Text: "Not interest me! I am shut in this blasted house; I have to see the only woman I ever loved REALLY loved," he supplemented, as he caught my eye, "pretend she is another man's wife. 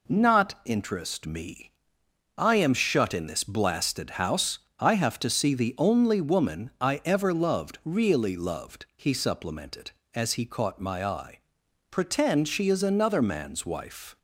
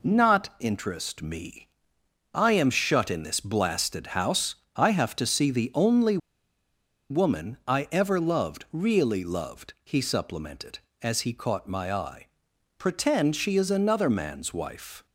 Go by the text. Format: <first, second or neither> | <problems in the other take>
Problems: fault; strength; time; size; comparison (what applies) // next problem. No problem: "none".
first | pauses between "only" and "woman"; noticeable; at 6.1 s; 0.93 s long